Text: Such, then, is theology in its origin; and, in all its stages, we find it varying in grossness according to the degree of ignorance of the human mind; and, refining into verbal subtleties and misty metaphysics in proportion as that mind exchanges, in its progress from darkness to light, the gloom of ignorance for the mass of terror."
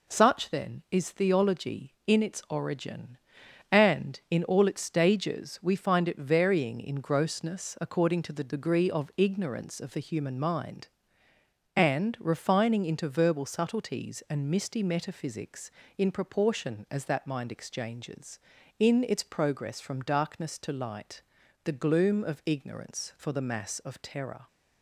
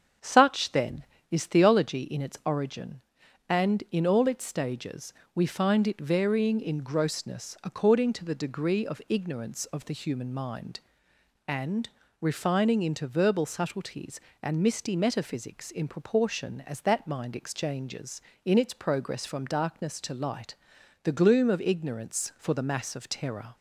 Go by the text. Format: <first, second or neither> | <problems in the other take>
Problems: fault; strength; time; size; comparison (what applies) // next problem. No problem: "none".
first | starts louder than the rest; strong; until 2.0 s; 7.5 dB